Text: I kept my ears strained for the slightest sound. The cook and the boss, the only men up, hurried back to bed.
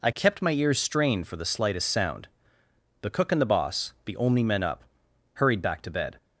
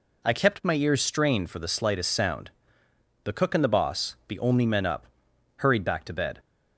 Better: neither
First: none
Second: none

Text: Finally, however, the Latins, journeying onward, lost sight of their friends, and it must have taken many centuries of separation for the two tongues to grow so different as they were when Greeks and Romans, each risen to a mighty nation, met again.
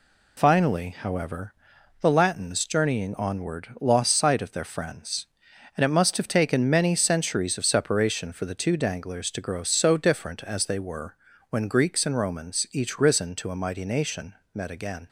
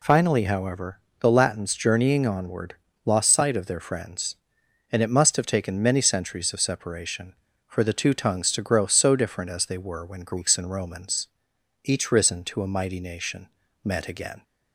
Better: second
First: says "danglers" for "tongues"; at 8.7 s // pauses between "were" and "when"; slight; at 11.1 s; 0.34 s long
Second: none

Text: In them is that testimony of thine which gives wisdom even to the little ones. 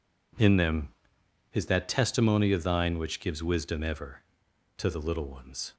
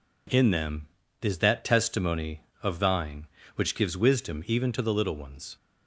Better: second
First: says "ever" for "even"; at 3.8 s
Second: none

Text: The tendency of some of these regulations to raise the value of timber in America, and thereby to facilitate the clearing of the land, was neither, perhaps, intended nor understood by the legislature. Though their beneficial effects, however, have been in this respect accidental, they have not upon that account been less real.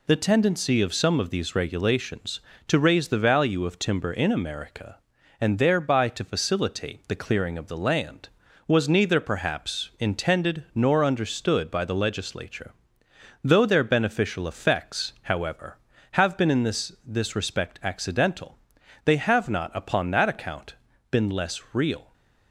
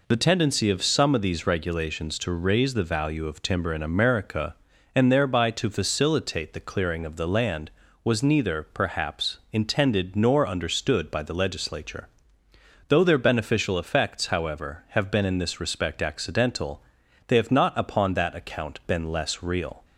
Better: second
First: says "this" twice; at 17.0 s // pauses between "account" and "been"; slight; at 20.7 s; 0.36 s long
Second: none

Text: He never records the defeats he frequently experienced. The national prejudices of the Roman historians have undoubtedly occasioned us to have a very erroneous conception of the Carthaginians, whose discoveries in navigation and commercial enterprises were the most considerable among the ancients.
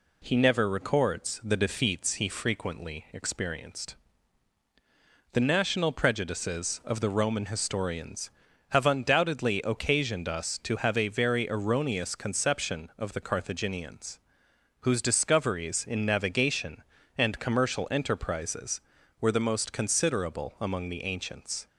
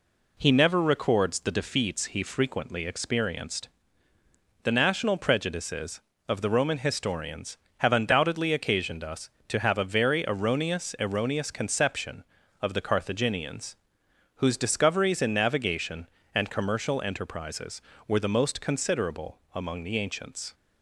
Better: first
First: none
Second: says "erroneous" twice; at 10.9 s // pauses between "considerable" and "among"; slight; at 19.3 s; 0.16 s long

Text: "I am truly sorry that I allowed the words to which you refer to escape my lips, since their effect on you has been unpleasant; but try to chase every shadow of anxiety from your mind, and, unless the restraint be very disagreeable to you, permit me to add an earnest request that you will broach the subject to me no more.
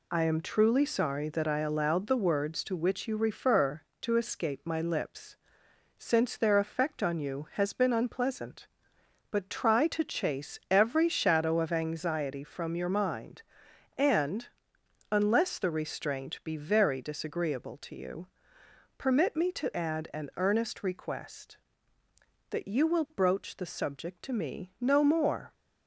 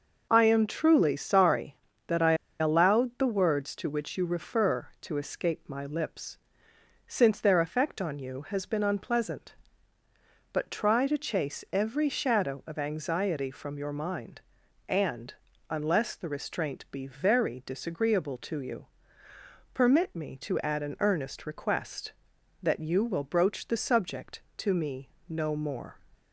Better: first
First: none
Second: pauses between "I" and "allowed"; slight; at 2.3 s; 0.25 s long // pauses between "me" and "no"; slight; at 25.0 s; 0.22 s long

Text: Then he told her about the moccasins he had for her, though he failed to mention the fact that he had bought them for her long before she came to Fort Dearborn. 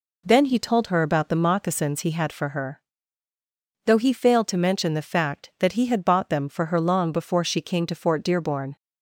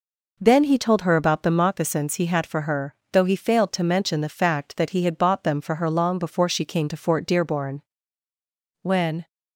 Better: first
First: none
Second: goes on to say "When"; slight; from 8.8 s on; 0.46 s long

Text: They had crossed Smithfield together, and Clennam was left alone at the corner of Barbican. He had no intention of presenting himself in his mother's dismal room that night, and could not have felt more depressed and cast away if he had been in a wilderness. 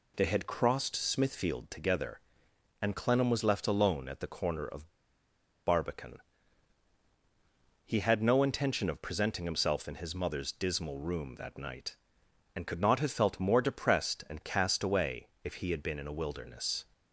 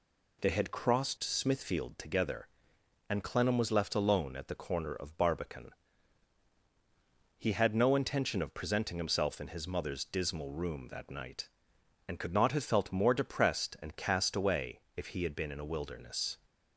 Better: second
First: pauses between "of" and "Barbican"; noticeable; at 4.8 s; 0.77 s long // pauses between "away" and "if"; slight; at 15.2 s; 0.16 s long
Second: pauses between "away" and "if"; slight; at 14.8 s; 0.16 s long

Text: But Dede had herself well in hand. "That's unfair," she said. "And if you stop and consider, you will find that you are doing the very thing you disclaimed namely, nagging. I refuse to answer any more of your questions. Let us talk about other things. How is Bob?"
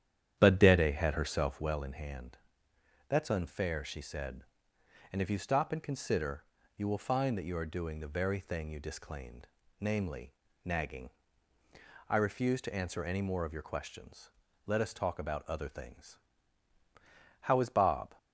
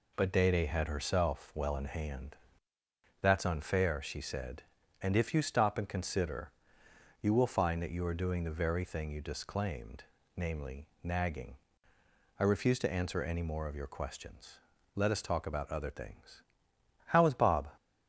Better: second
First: starts louder than the rest; strong; until 1.8 s; 10 dB // pauses between "disclaimed" and "namely"; slight; at 9.4 s; 0.32 s long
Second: pauses between "disclaimed" and "namely"; slight; at 10.0 s; 0.32 s long

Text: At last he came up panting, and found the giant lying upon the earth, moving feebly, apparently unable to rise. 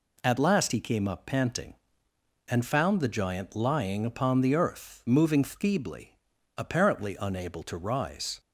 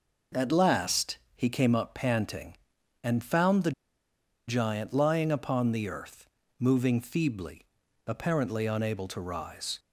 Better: first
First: none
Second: pauses between "last" and "he"; slight; at 1.1 s; 0.16 s long // pauses between "the" and "giant"; noticeable; at 3.7 s; 0.76 s long

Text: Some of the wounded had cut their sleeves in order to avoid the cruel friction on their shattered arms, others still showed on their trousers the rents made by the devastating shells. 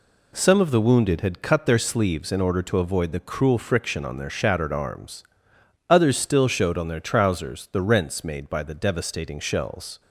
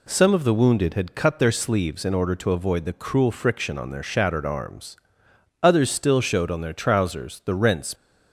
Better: first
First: none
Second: stops before "made by the devastating shells"; at 7.9 s

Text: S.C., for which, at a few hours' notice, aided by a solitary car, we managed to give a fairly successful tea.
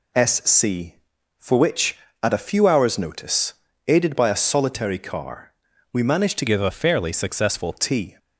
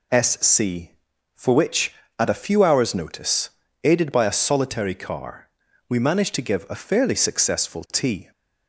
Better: second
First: changes voice from "give" to "successful"; from 6.4 to 7.7 s; 1.3 s long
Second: none

